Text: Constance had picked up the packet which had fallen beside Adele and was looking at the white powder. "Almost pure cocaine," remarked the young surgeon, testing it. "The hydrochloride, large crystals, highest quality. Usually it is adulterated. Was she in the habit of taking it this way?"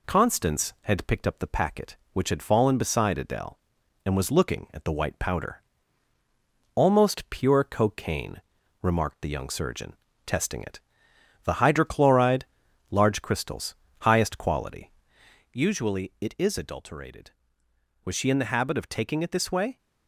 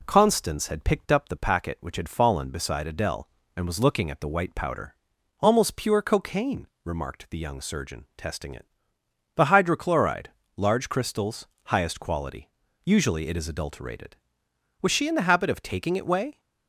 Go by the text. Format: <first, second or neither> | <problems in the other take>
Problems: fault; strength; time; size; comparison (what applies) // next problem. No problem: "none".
first | skips "this"; at 16.0 s